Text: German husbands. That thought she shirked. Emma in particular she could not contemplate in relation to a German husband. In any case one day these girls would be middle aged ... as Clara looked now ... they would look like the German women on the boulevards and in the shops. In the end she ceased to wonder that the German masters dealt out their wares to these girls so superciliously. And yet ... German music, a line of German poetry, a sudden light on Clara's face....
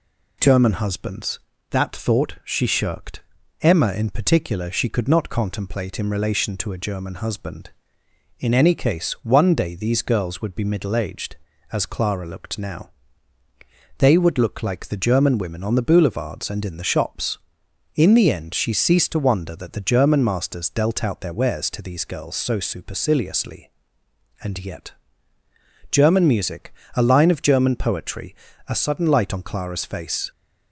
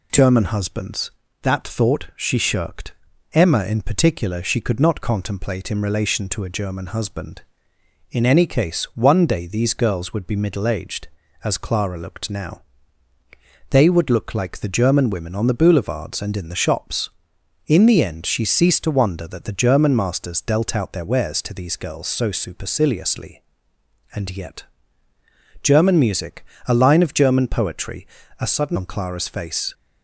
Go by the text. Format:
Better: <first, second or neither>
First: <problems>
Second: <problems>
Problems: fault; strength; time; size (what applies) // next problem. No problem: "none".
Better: first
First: none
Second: skips "light"; at 28.7 s